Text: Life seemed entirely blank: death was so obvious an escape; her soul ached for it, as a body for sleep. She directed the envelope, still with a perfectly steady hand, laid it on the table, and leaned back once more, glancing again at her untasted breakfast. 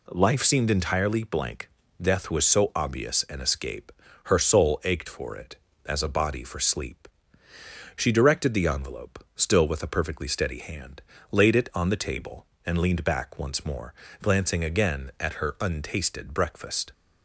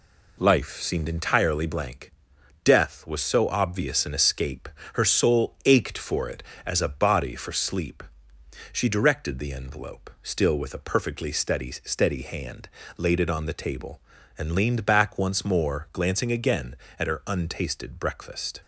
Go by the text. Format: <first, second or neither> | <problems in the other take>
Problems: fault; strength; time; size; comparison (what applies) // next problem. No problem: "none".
first | says "steady" twice; at 11.7 s